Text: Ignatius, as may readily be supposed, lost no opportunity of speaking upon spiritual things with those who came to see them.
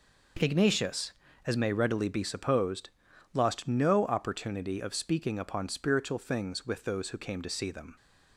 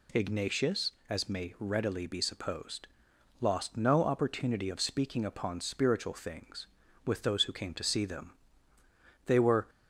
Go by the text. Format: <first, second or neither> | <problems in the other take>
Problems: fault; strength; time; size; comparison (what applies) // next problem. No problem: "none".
first | goes on to say "They were"; slight; from 9.2 s on; 0.44 s long